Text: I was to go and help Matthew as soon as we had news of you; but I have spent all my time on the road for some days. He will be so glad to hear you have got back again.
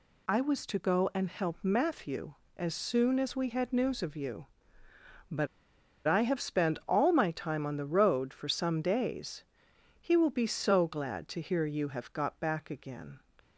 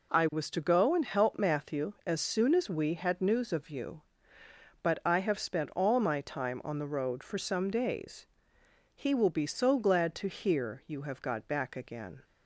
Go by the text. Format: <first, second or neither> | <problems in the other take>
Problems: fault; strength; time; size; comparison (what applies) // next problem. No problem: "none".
second | pauses between "but" and "I"; noticeable; at 5.4 s; 0.61 s long